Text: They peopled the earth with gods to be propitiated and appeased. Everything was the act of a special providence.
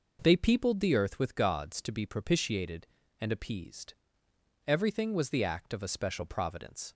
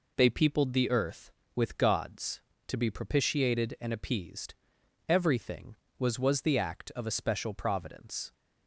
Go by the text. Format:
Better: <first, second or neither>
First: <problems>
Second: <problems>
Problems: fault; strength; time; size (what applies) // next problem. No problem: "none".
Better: first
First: none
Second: says "was" twice; at 6.1 s